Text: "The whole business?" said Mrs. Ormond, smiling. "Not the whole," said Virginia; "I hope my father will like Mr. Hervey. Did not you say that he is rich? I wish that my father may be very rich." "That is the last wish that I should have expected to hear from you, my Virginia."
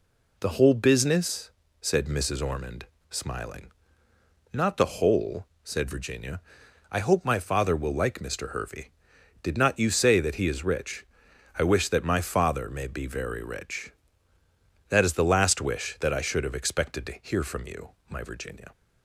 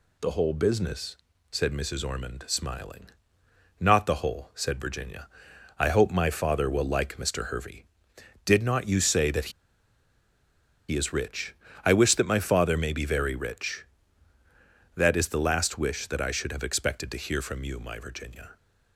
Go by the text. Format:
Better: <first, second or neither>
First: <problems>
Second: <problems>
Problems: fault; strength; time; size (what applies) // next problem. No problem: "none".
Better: first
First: none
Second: pauses between "that" and "he"; strong; at 9.5 s; 1.3 s long